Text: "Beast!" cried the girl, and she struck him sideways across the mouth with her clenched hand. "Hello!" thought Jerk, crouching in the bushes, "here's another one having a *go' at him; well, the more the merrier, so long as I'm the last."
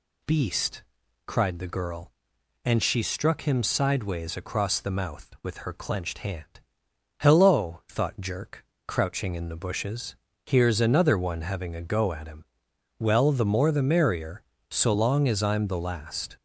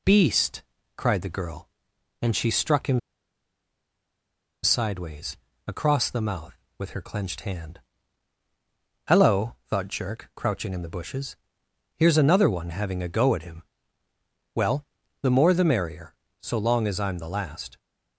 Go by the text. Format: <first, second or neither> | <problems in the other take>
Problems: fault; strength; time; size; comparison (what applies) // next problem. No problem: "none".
first | pauses between "him" and "sideways"; strong; at 2.9 s; 1.6 s long // pauses between "sideways" and "across"; slight; at 5.3 s; 0.28 s long